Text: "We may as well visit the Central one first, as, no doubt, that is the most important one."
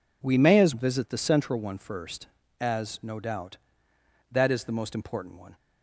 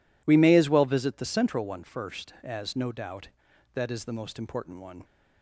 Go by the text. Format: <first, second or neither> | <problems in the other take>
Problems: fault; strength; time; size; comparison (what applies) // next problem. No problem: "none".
second | skips "well"; at 0.7 s